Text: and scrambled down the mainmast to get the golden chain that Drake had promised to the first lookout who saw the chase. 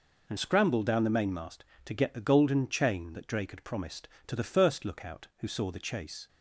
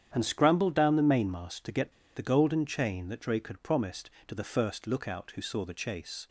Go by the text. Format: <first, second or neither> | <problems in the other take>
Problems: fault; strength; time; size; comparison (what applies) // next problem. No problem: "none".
first | starts louder than the rest; strong; until 1.1 s; 9.5 dB // pauses between "get" and "the"; slight; at 1.9 s; 0.23 s long